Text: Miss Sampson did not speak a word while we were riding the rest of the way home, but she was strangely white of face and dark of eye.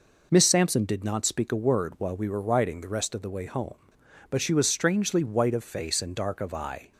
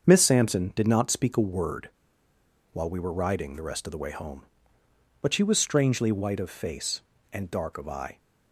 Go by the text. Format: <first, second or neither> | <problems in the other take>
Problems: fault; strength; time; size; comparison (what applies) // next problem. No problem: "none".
first | starts louder than the rest; until 1.1 s; 6.5 dB // pauses between "word" and "while"; noticeable; at 1.8 s; 0.83 s long